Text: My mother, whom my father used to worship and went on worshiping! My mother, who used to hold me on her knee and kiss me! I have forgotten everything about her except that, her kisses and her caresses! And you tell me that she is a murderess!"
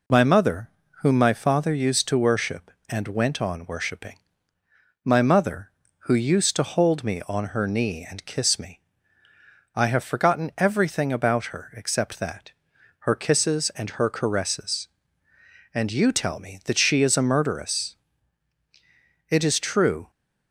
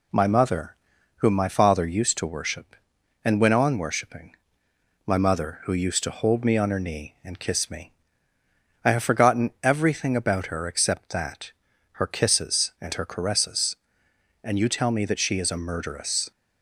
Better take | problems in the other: second | goes on to say "It is true"; noticeable; from 19.2 s on; 0.82 s long

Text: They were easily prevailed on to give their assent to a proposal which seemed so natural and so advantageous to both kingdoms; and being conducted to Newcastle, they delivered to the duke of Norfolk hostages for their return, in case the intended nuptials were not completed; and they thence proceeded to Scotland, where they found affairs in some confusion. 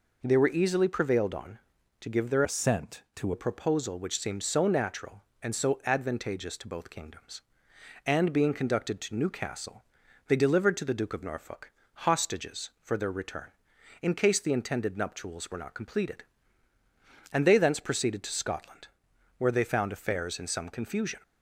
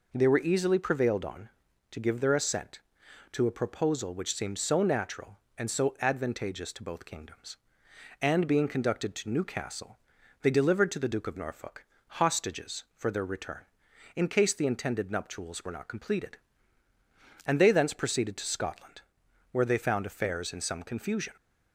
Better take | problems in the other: second | changes voice from "assent" to "to"; from 2.4 to 3.3 s; 0.9 s long // pauses between "Norfolk" and "hostages"; slight; at 11.7 s; 0.28 s long; slight in the second

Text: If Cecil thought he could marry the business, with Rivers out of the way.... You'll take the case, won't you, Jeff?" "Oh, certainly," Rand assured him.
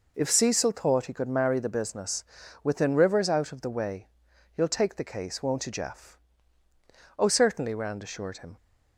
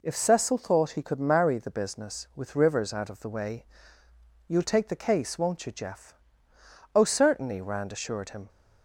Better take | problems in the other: second | says "within" for "with"; at 2.6 s

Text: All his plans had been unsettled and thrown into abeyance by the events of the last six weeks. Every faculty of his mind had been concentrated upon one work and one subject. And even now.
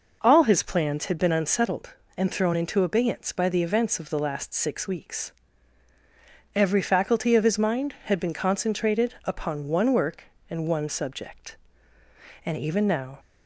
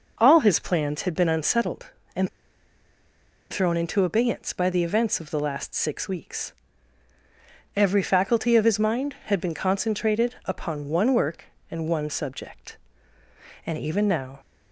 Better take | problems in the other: first | pauses between "and" and "thrown"; at 2.2 s; 1.2 s long

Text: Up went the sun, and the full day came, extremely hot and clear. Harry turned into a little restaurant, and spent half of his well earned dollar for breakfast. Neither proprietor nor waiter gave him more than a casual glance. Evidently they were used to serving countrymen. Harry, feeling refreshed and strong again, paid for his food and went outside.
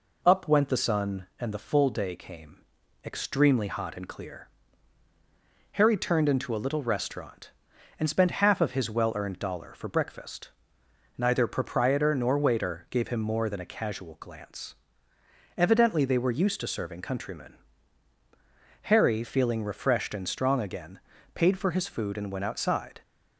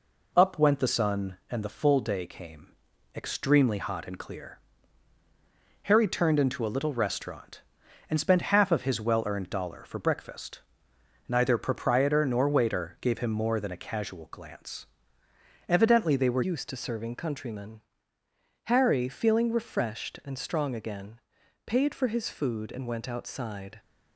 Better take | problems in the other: first | changes voice at "used"; from 16.4 s on; 7.3 s long

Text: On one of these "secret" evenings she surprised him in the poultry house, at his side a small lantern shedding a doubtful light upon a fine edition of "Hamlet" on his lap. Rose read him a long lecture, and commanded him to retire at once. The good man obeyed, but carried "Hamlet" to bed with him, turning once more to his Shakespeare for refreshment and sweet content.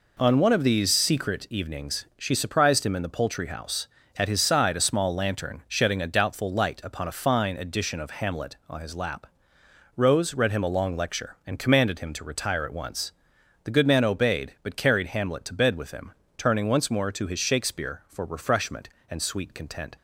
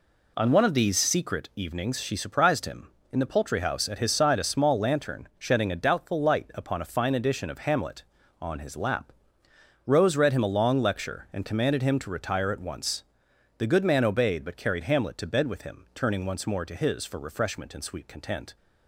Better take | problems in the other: first | skips "Shakespeare"; at 17.0 s

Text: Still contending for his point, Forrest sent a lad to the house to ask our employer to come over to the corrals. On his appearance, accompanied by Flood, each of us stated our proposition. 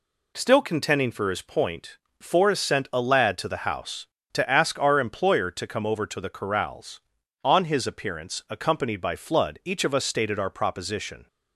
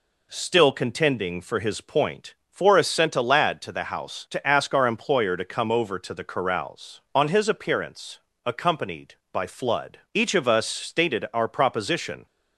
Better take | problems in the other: neither | none

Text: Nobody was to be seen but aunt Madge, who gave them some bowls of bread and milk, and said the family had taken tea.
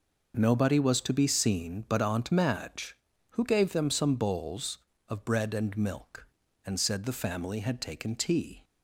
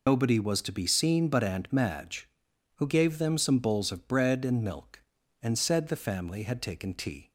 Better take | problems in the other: first | loses the start of "Nobody"; at 0.0 s; 125 ms

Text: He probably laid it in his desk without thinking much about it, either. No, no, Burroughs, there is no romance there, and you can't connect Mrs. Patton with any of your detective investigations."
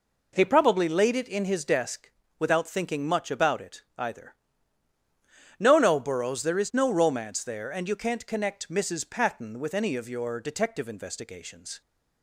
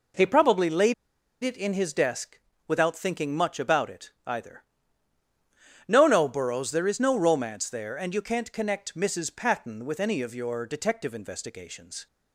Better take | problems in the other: first | pauses between "laid" and "it"; noticeable; at 0.9 s; 0.48 s long // pauses between "desk" and "without"; slight; at 2.3 s; 0.30 s long; slight in the first

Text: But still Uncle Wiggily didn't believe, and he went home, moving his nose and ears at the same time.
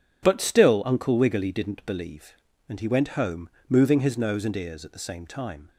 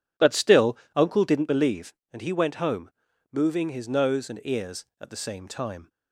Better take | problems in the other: first | pauses between "still" and "Uncle"; slight; at 0.7 s; 0.18 s long // skips "Wiggily"; at 1.2 s

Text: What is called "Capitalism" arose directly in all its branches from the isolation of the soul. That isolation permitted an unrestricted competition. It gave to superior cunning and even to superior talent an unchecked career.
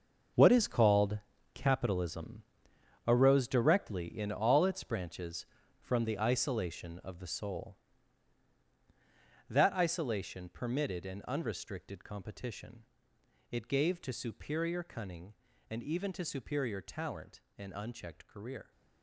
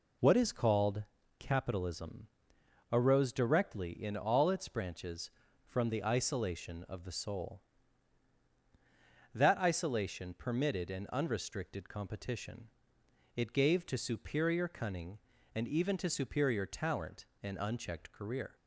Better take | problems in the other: second | gets quieter; strong; throughout; 12 dB // pauses between "called" and "Capitalism"; slight; at 1.1 s; 0.36 s long; slight in the second // pauses between "Capitalism" and "arose"; noticeable; at 2.4 s; 0.62 s long; noticeable in the second // pauses between "talent" and "an"; slight; at 17.4 s; 0.18 s long; slight in the second

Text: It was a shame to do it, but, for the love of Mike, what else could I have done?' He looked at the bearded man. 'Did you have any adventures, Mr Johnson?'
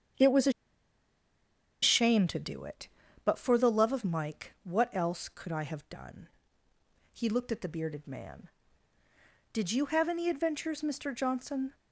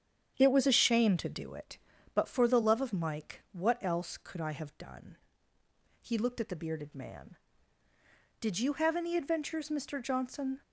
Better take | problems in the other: second | starts louder than the rest; strong; until 2.4 s; 8 dB; strong in the second // pauses between "a" and "shame"; strong; at 0.5 s; 1.3 s long

